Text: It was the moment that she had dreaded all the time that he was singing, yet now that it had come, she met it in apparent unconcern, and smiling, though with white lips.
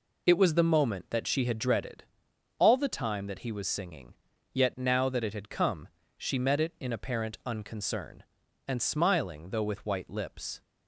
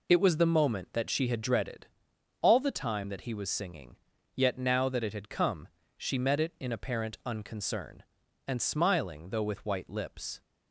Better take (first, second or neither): neither